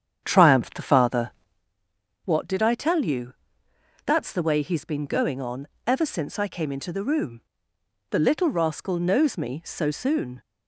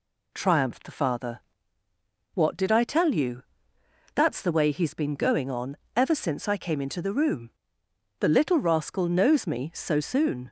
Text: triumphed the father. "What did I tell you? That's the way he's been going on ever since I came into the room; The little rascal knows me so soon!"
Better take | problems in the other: second | starts louder than the rest; strong; until 1.7 s; 8.5 dB // pauses between "on" and "ever"; slight; at 5.6 s; 0.18 s long; slight in the second

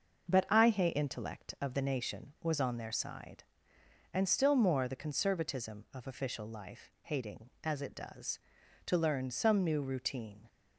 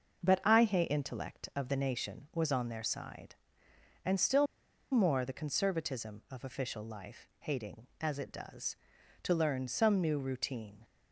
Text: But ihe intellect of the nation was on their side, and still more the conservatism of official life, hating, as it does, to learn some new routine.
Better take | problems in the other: first | starts louder than the rest; noticeable; until 1.2 s; 6 dB; noticeable in the first // pauses between "still" and "more"; noticeable; at 4.4 s; 0.46 s long

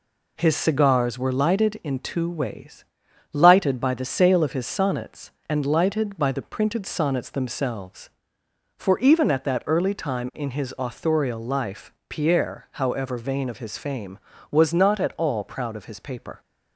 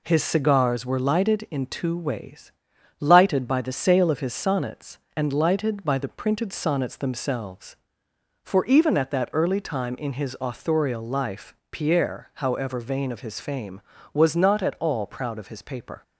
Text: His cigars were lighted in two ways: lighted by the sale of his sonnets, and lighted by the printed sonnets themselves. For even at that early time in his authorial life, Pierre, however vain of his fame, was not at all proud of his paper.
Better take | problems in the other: neither | none

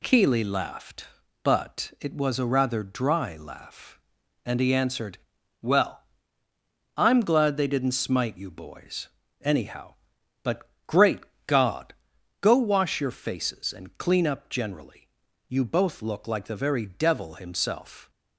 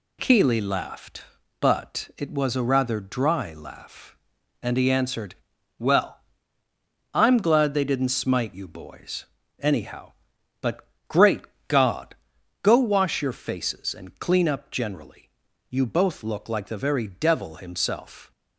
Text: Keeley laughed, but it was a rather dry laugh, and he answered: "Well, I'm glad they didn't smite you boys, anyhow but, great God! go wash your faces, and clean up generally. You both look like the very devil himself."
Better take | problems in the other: neither | pauses between "great" and "God"; slight; the same in both

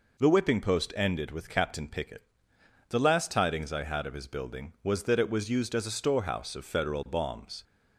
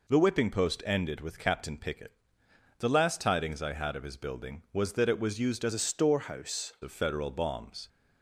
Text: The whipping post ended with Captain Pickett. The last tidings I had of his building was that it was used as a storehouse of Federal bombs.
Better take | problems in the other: first | changes voice from "a" to "storehouse"; from 5.7 to 6.7 s; 1.0 s long

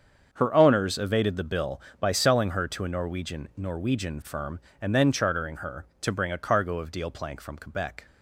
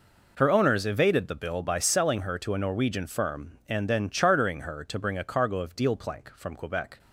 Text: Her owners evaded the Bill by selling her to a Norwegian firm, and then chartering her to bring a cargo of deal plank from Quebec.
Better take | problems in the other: second | starts louder than the rest; until 1.3 s; 7 dB // says "Norwegian" twice; at 3.5 s

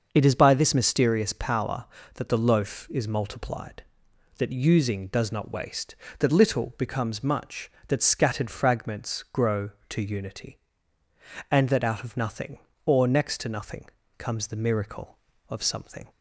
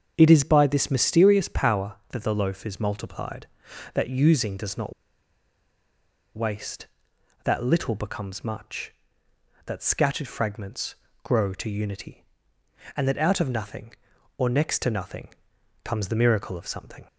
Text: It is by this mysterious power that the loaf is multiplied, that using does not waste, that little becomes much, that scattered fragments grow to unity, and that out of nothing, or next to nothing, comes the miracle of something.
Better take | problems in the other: first | starts louder than the rest; until 1.1 s; 7 dB; noticeable in the first // pauses between "not" and "waste"; strong; at 4.9 s; 1.4 s long // pauses between "fragments" and "grow"; slight; at 10.9 s; 0.30 s long

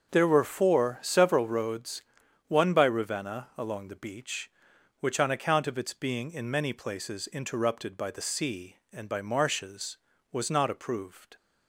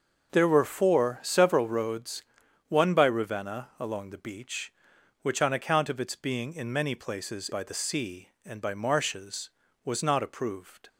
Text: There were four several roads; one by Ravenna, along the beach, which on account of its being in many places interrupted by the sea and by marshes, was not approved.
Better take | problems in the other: first | starts louder than the rest; until 1.3 s; 6 dB; also in the first // skips "interrupted"; at 7.5 s

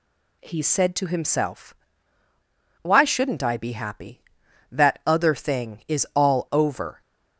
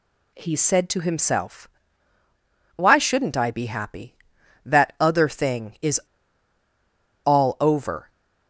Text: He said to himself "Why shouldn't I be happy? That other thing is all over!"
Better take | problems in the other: first | pauses between "himself" and "Why"; at 1.6 s; 1.1 s long; also in the first // pauses between "is" and "all"; strong; at 5.9 s; 1.2 s long

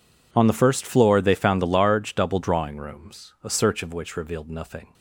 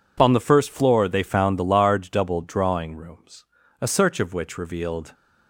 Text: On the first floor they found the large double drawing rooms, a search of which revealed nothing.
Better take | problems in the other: first | stops before "nothing"; at 5.1 s

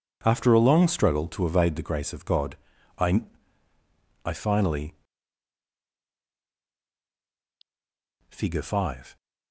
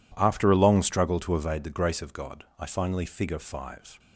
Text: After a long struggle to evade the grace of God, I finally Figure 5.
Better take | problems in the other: second | says "I" twice; at 4.2 s // pauses between "finally" and "Figure"; strong; at 4.9 s; 3.3 s long

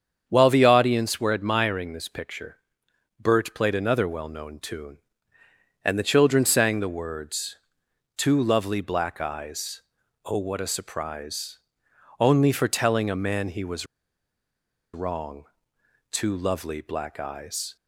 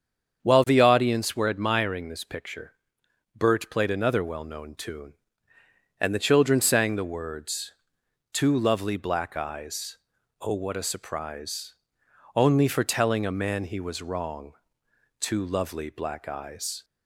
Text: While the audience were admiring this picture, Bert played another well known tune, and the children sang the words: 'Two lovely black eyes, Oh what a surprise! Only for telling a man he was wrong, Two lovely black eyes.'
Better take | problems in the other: second | starts louder than the rest; strong; until 1.2 s; 7.5 dB; strong in the second // pauses between "was" and "wrong"; at 13.8 s; 1.0 s long

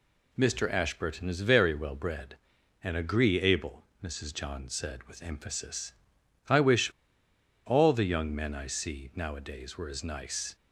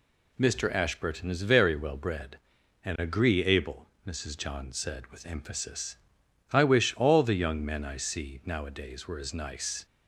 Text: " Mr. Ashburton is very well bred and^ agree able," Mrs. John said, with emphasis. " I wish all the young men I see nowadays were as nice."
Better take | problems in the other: second | pauses between "wish" and "all"; noticeable; at 6.8 s; 0.76 s long

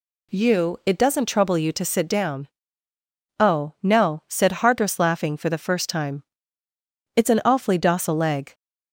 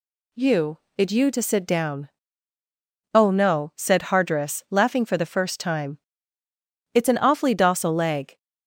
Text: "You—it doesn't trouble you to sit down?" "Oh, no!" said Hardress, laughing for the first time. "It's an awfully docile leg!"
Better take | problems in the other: first | skips "doesn't trouble"; at 1.0 s

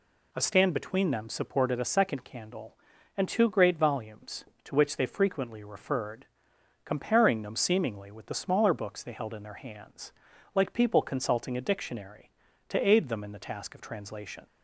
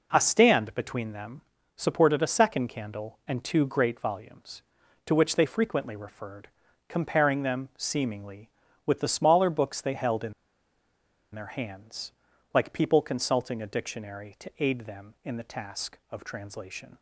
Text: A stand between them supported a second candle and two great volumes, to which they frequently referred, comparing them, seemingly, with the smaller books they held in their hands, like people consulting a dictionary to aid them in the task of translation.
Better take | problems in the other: first | pauses between "them" and "supported"; at 1.3 s; 0.38 s long // pauses between "in" and "their"; at 10.3 s; 1.0 s long

